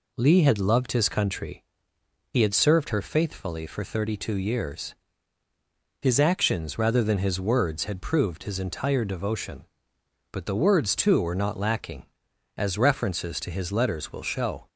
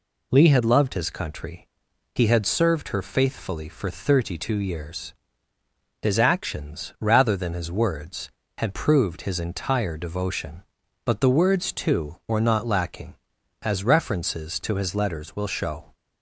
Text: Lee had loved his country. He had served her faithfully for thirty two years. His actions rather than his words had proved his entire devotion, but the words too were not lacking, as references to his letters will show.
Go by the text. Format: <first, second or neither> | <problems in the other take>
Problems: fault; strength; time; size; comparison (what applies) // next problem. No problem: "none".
neither | none